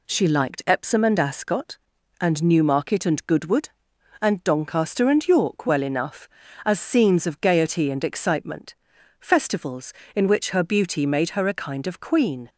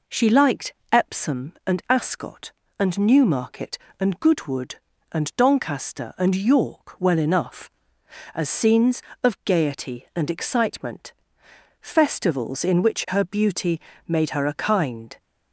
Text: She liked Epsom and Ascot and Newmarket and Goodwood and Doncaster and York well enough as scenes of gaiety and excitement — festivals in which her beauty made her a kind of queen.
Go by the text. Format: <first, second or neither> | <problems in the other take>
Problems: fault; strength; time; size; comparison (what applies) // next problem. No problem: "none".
first | pauses between "liked" and "Epsom"; slight; at 0.7 s; 0.20 s long // pauses between "beauty" and "made"; slight; at 13.7 s; 0.28 s long // stops before "of queen"; at 15.1 s